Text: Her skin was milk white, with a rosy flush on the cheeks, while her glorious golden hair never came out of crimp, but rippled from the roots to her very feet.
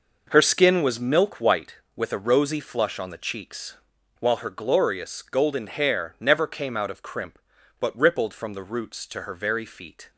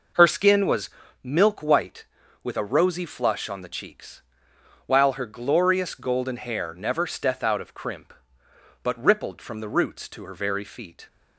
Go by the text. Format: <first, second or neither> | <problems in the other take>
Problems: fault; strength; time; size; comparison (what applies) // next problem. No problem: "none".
first | pauses between "was" and "milk"; slight; at 0.8 s; 0.34 s long // says "steth" for "came"; at 7.0 s